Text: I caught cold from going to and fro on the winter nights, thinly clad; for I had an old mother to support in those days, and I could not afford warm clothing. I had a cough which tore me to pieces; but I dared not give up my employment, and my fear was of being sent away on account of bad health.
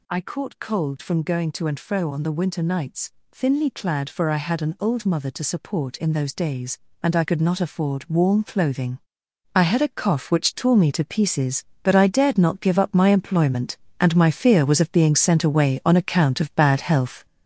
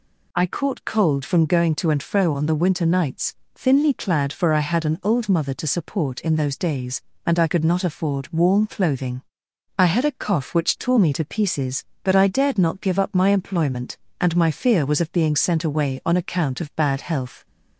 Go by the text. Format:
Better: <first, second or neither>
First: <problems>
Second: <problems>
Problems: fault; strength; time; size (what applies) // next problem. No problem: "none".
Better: second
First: gets louder; throughout; 6 dB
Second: none